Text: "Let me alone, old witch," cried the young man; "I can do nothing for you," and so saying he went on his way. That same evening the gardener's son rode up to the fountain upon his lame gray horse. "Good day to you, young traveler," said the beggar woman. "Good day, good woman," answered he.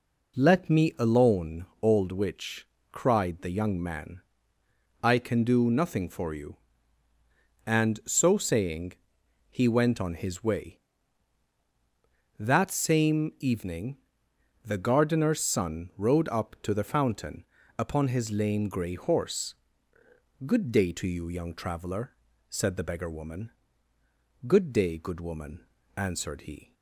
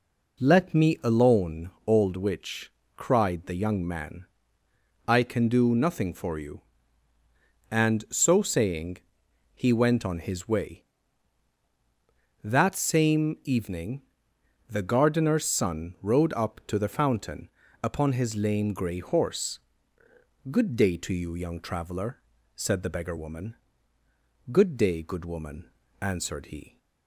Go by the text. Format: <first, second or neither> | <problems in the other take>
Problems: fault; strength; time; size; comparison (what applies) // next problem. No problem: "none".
neither | pauses between "saying" and "he"; noticeable; the same in both // pauses between "evening" and "the"; noticeable; the same in both // pauses between "fountain" and "upon"; slight; the same in both